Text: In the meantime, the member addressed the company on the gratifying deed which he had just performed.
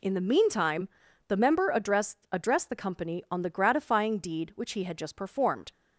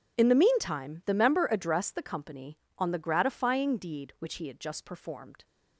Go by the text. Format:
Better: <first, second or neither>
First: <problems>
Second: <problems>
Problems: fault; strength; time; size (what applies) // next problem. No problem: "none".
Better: second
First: says "addressed" twice; at 2.3 s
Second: none